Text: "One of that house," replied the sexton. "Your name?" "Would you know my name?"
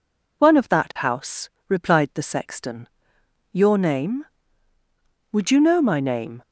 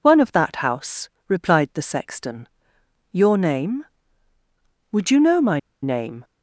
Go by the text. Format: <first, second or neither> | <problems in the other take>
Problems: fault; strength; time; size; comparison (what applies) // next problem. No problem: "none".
first | pauses between "my" and "name"; slight; at 5.5 s; 0.23 s long